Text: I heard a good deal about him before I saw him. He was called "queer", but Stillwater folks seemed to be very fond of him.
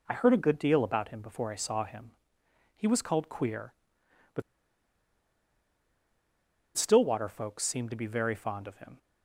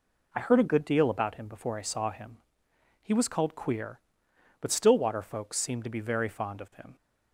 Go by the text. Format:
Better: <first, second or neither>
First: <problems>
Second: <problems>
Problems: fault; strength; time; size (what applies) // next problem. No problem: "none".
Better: second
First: pauses between "but" and "Stillwater"; strong; at 4.4 s; 2.3 s long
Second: none